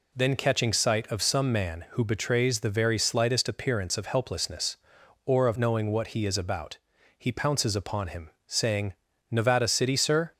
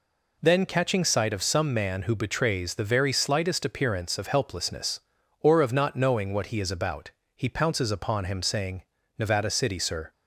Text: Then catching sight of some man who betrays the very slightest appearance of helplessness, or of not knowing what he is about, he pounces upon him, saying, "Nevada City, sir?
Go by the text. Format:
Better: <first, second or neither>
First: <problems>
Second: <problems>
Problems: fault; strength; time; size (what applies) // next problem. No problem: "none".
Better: second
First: skips "not"; at 5.5 s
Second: none